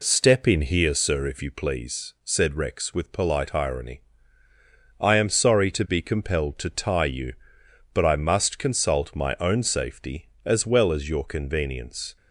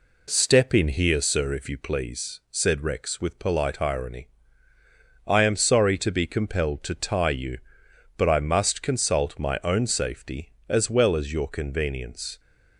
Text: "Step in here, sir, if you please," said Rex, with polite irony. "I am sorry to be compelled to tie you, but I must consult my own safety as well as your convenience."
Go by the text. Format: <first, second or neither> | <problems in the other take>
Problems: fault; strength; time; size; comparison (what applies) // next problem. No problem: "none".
neither | none